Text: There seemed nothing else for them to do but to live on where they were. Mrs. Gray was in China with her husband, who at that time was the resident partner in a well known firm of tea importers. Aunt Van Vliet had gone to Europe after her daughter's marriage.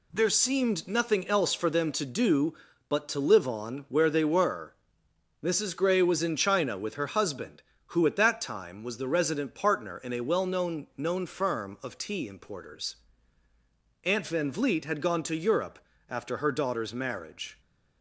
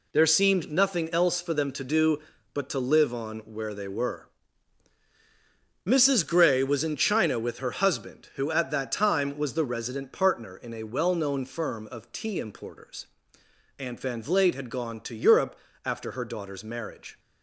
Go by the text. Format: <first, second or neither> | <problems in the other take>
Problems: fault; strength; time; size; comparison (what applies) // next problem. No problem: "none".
second | says "known" twice; at 10.9 s // pauses between "Europe" and "after"; slight; at 15.7 s; 0.30 s long; slight in the second